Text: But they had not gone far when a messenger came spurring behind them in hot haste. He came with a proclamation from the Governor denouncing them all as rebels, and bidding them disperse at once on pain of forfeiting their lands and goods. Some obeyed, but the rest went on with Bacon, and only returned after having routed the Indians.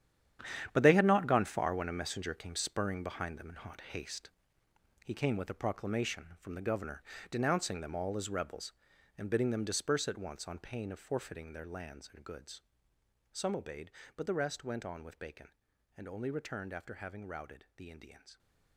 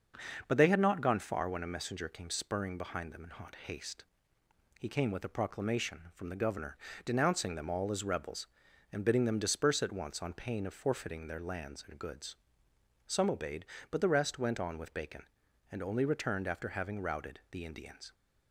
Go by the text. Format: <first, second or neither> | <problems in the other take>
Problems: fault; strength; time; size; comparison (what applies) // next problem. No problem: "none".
second | gets quieter; strong; throughout; 12 dB // starts louder than the rest; strong; until 1.7 s; 9.5 dB; also in the second // pauses between "Governor" and "denouncing"; slight; at 7.0 s; 0.28 s long; slight in the second